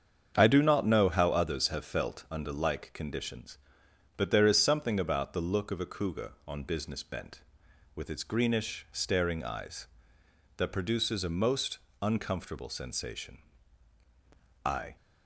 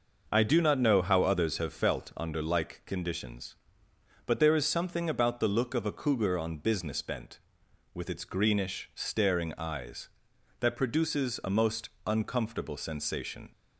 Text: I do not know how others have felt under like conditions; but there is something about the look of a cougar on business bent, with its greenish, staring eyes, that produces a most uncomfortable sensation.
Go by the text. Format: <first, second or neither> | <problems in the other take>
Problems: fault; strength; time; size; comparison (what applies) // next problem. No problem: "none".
second | starts louder than the rest; strong; until 1.3 s; 7.5 dB // pauses between "most" and "uncomfortable"; slight; at 11.7 s; 0.24 s long // goes on to say "I"; slight; from 14.6 s on; 0.30 s long